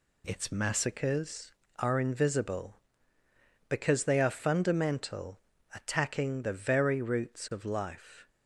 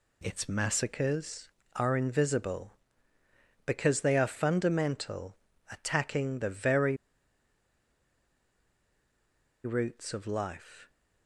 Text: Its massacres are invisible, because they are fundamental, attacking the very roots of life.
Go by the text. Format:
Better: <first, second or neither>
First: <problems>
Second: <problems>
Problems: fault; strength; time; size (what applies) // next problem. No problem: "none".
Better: first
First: none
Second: pauses between "very" and "roots"; strong; at 6.9 s; 2.6 s long